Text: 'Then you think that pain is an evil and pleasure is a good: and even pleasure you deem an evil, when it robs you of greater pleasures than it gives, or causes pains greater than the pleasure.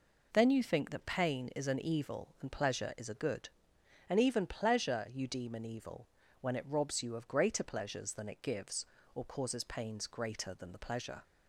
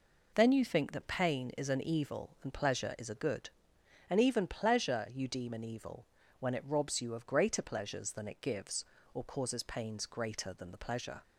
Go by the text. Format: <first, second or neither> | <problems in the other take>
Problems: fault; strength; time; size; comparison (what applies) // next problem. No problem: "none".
neither | none